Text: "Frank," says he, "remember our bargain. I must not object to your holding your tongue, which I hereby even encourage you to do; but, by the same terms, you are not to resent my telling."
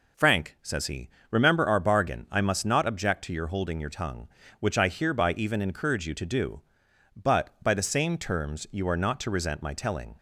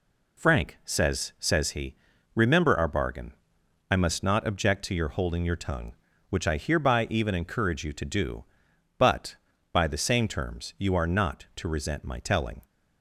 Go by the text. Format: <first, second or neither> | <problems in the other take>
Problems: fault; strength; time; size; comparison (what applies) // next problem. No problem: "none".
first | says "says" twice; at 1.4 s